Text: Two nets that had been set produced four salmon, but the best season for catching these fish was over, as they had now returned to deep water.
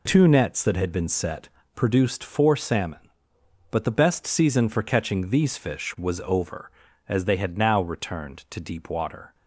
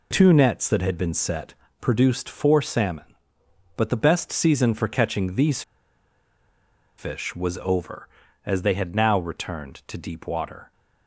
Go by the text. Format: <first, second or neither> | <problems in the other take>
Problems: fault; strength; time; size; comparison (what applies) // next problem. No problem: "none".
first | pauses between "set" and "produced"; slight; at 1.5 s; 0.26 s long; slight in the first // pauses between "these" and "fish"; strong; at 5.6 s; 1.3 s long